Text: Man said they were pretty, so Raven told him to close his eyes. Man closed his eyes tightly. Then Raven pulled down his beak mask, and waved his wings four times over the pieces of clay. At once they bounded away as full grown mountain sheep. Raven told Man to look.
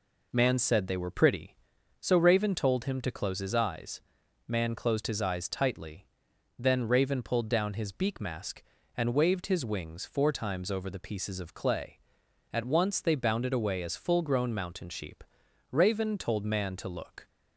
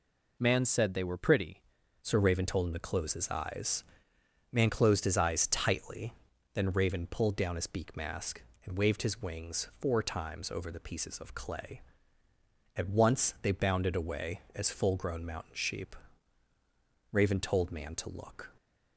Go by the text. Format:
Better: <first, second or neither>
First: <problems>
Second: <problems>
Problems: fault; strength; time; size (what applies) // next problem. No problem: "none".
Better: first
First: none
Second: changes voice at "so"; from 2.0 s on; 16.4 s long